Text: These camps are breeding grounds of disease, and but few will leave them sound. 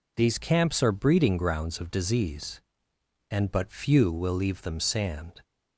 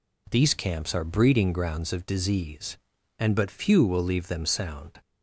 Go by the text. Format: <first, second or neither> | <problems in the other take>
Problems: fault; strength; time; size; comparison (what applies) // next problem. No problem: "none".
second | says "sand" for "sound"; at 4.7 s